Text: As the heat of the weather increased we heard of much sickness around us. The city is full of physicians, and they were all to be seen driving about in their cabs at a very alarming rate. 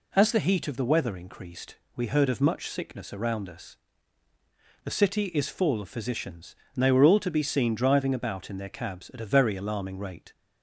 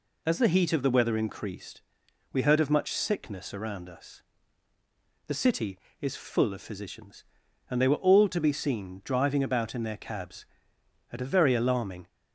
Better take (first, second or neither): first